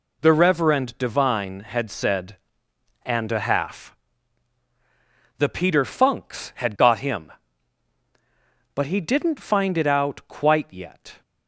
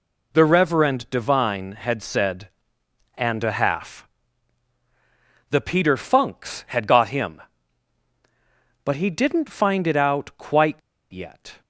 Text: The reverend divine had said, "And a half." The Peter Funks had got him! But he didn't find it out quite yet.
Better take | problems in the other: first | pauses between "quite" and "yet"; slight; at 10.7 s; 0.33 s long

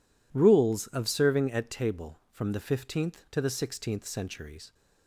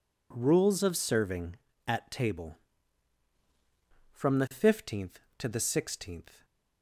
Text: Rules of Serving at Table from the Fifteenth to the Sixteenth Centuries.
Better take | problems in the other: first | stops before "Centuries"; at 6.4 s

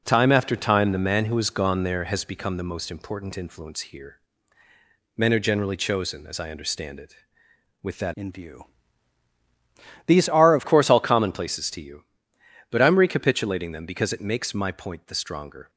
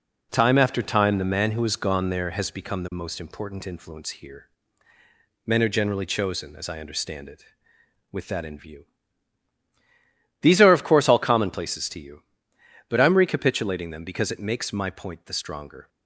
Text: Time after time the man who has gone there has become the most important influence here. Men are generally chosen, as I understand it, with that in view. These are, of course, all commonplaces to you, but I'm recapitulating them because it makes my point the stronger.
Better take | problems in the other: second | changes voice from "in" to "of"; from 8.1 to 10.6 s; 2.5 s long

